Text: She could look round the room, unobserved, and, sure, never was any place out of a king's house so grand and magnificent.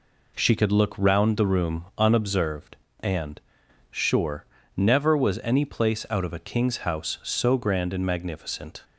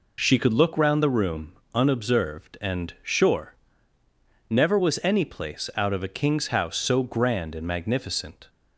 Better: neither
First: none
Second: none

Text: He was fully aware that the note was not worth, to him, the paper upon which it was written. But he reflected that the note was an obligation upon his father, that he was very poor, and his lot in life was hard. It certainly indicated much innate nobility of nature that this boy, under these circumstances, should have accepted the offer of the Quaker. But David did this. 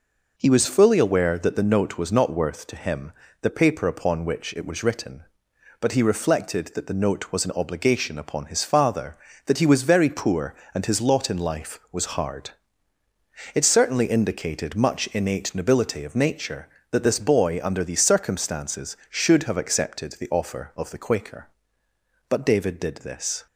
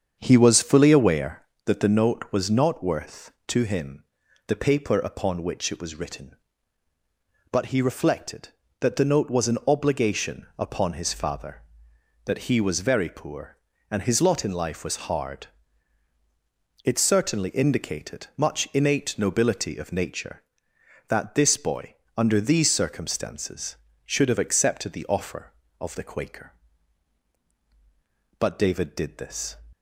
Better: first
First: none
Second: starts louder than the rest; strong; until 1.5 s; 7.5 dB

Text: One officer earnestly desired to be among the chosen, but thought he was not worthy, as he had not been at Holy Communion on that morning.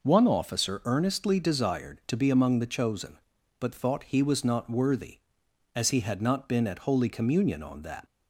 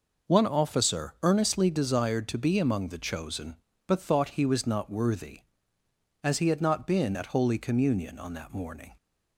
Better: second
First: stops before "morning"; at 8.0 s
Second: none

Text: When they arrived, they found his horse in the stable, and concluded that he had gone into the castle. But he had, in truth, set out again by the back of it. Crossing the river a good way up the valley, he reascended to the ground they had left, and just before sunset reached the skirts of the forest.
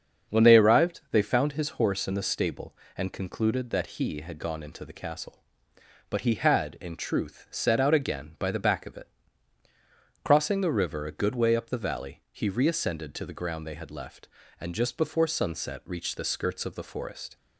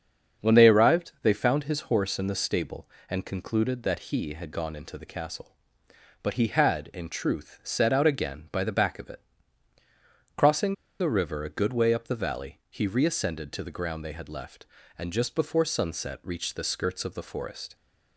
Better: first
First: starts louder than the rest; until 1.3 s; 7 dB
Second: starts louder than the rest; until 1.5 s; 7 dB // pauses between "Crossing" and "the"; slight; at 10.7 s; 0.27 s long

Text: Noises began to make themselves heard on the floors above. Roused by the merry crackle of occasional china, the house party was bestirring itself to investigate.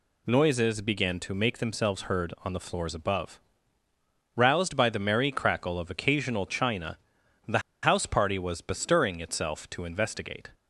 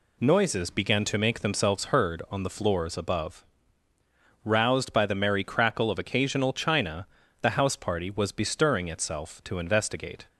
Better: second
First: pauses between "the" and "house"; slight; at 7.5 s; 0.24 s long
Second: none

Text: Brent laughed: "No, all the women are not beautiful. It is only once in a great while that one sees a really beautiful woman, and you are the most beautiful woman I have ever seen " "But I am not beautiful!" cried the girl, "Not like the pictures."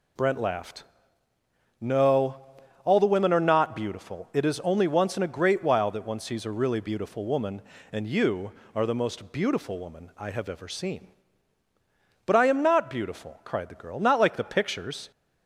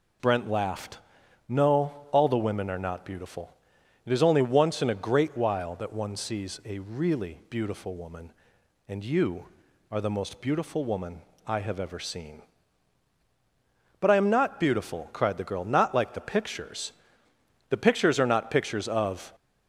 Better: first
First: none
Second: pauses between "woman" and "I"; slight; at 11.2 s; 0.24 s long // goes on to say "The pictures are not pictures of"; from 17.6 s on; 1.6 s long

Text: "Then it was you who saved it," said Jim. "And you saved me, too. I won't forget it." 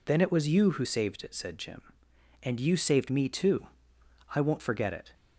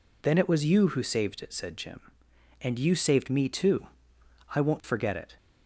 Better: neither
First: none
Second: none

